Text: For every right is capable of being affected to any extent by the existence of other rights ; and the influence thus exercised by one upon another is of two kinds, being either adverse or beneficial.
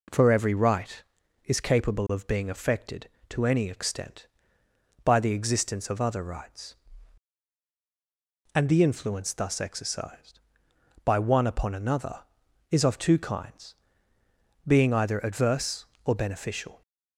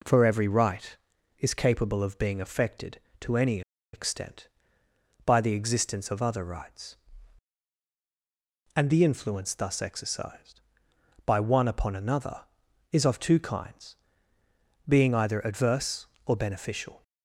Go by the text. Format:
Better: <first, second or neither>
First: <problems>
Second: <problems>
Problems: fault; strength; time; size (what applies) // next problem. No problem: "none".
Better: first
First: none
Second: pauses between "any" and "extent"; slight; at 3.6 s; 0.32 s long